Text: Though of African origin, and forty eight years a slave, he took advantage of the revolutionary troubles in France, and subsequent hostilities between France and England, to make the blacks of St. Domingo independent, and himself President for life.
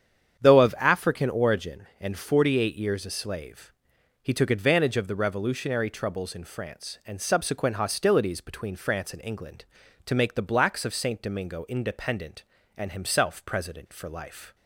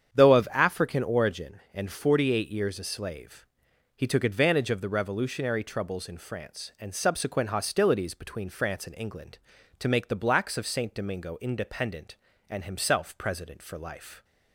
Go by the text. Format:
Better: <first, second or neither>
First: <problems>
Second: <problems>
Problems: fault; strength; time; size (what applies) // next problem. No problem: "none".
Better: neither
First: starts louder than the rest; strong; until 1.4 s; 8 dB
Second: starts louder than the rest; strong; until 1.1 s; 8 dB